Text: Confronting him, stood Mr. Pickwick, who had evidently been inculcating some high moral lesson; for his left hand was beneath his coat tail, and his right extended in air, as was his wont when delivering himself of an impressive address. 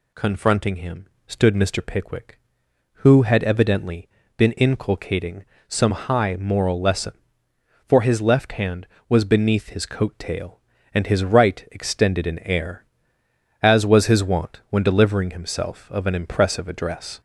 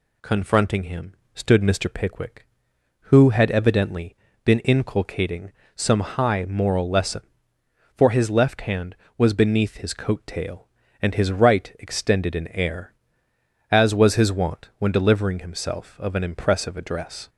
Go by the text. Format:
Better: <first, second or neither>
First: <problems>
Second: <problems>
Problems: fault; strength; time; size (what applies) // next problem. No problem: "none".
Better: second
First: gets louder; slight; throughout; 3 dB // pauses between "evidently" and "been"; slight; at 4.0 s; 0.28 s long // pauses between "inculcating" and "some"; slight; at 5.4 s; 0.24 s long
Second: pauses between "evidently" and "been"; slight; at 4.1 s; 0.28 s long // pauses between "inculcating" and "some"; slight; at 5.5 s; 0.24 s long